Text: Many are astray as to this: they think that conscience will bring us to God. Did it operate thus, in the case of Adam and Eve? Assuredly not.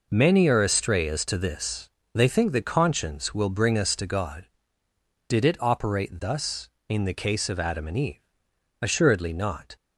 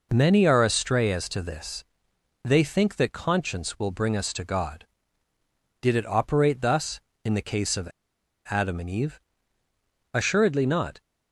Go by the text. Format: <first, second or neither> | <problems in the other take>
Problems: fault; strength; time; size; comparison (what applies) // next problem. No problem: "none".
first | pauses between "of" and "Adam"; noticeable; at 7.9 s; 0.58 s long